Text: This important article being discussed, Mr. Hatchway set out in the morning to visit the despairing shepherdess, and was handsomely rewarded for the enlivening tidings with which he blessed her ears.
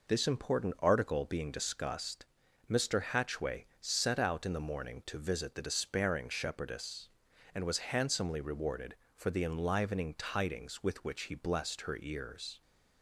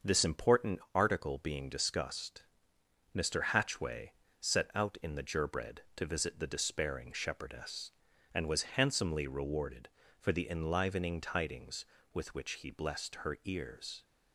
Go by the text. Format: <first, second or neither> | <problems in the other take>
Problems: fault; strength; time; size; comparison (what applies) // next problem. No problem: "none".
first | starts louder than the rest; until 1.1 s; 6.5 dB // pauses between "important" and "article"; slight; at 0.7 s; 0.16 s long // pauses between "Hatchway" and "set"; slight; at 4.1 s; 0.26 s long // says "gerbread" for "morning"; at 5.2 s